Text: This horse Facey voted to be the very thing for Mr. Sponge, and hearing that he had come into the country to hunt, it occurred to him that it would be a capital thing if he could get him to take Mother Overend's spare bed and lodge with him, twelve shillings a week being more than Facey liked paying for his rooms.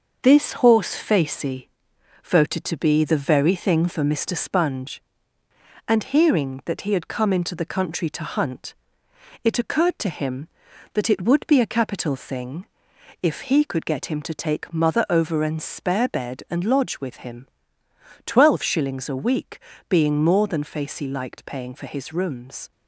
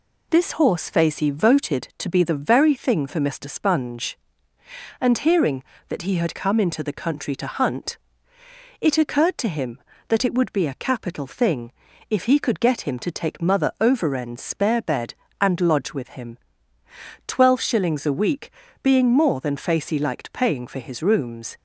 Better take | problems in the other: second | gets quieter; noticeable; throughout; 4.5 dB // pauses between "Facey" and "voted"; noticeable; at 1.6 s; 0.54 s long // pauses between "thing" and "if"; noticeable; at 12.6 s; 0.56 s long; also in the second // pauses between "week" and "being"; slight; at 19.5 s; 0.28 s long; slight in the second

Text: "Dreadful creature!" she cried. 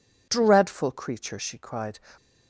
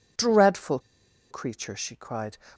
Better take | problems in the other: first | pauses between "Dreadful" and "creature"; noticeable; at 0.7 s; 0.50 s long

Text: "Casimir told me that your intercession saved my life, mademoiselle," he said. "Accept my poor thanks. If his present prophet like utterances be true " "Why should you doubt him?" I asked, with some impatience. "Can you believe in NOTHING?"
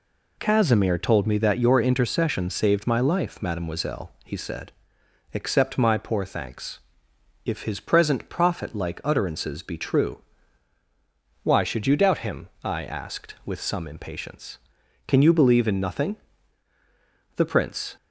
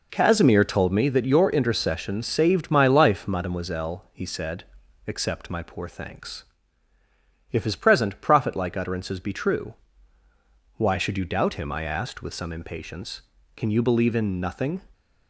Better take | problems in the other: second | goes on to say "The Prince"; noticeable; from 17.3 s on; 0.62 s long

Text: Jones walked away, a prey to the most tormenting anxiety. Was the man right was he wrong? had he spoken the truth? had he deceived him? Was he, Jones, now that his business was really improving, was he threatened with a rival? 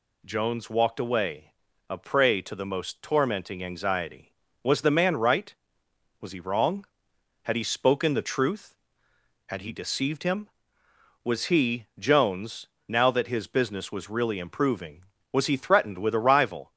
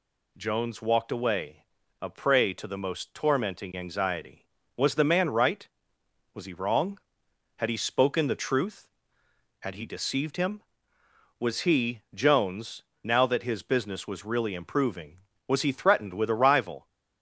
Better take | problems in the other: neither | none

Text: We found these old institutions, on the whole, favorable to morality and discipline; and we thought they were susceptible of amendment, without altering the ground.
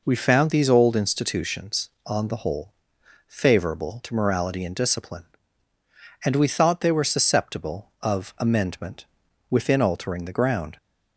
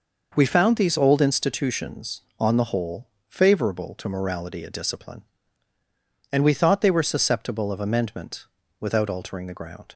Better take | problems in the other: second | says "within" for "without"; at 9.4 s

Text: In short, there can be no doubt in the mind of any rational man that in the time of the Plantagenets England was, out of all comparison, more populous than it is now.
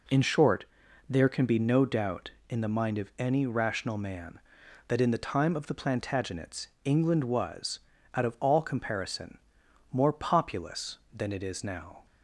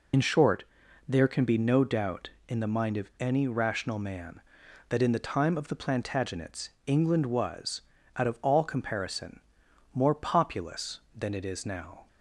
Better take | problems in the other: first | loses the start of "In"; at 0.1 s; 65 ms // pauses between "Plantagenets" and "England"; slight; at 6.6 s; 0.16 s long; slight in the first

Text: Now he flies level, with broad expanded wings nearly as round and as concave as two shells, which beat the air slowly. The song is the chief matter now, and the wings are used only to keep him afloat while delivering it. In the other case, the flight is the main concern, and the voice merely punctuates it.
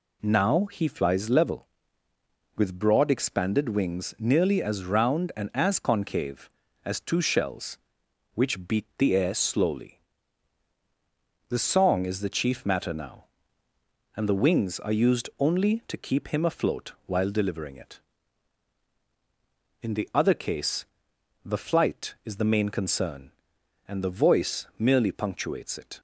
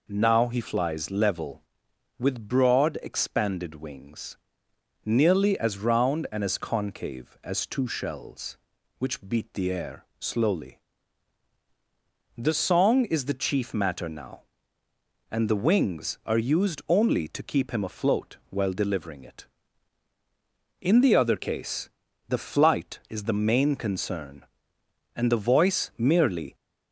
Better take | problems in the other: first | pauses between "wings" and "nearly"; noticeable; at 4.3 s; 0.68 s long // pauses between "air" and "slowly"; slight; at 10.0 s; 0.16 s long // stops before "punctuates it"; at 26.5 s

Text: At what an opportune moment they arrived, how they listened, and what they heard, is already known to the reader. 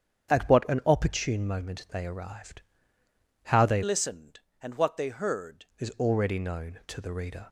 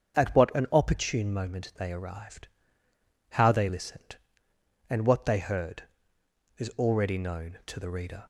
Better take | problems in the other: second | starts louder than the rest; strong; until 1.3 s; 8 dB; also in the second // changes voice from "listened" to "heard"; from 3.8 to 5.6 s; 1.8 s long

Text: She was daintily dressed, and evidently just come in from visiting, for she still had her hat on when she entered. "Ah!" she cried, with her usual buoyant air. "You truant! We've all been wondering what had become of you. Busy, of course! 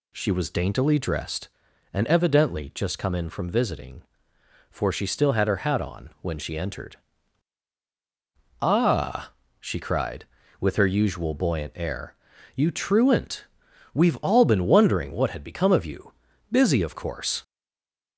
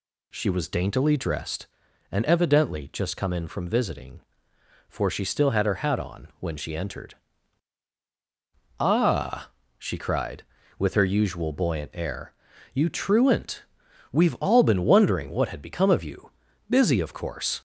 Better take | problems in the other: second | stays silent after the last word; slight; from 17.4 s on; 0.7 s long

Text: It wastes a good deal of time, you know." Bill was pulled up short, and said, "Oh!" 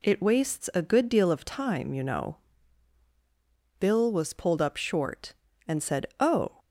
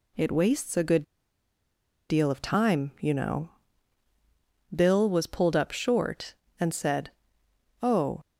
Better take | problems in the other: first | pauses between "good" and "deal"; at 1.0 s; 1.0 s long

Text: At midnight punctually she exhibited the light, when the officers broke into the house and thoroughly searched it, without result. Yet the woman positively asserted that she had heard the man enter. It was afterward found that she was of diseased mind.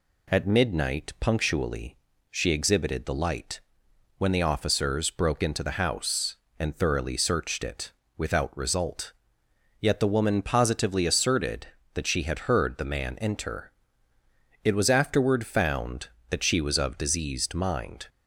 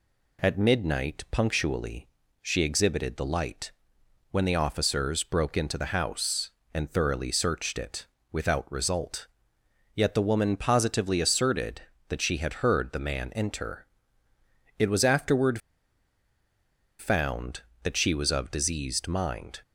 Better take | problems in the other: first | pauses between "punctually" and "she"; slight; at 2.0 s; 0.34 s long; slight in the first // pauses between "afterward" and "found"; strong; at 15.5 s; 1.3 s long

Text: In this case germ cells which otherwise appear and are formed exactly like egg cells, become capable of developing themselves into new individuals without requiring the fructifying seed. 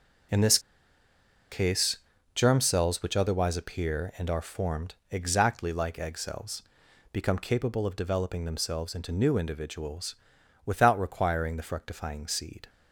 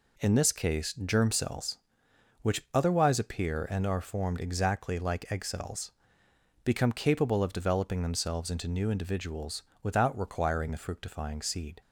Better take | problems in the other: second | starts louder than the rest; until 2.6 s; 6.5 dB // pauses between "this" and "case"; noticeable; at 0.5 s; 0.92 s long // pauses between "case" and "germ"; slight; at 1.9 s; 0.36 s long // pauses between "formed" and "exactly"; slight; at 4.9 s; 0.16 s long // pauses between "individuals" and "without"; noticeable; at 10.1 s; 0.50 s long; slight in the second

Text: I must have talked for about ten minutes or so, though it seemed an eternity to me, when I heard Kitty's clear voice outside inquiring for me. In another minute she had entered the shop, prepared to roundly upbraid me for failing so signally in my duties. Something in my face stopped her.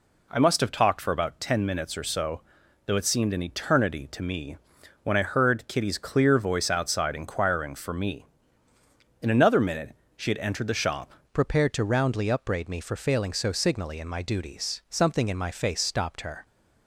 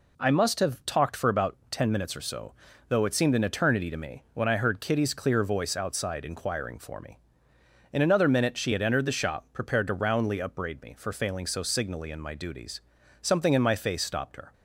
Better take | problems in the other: second | pauses between "minute" and "she"; slight; at 9.9 s; 0.22 s long // changes voice at "prepared"; from 11.3 s on; 5.1 s long

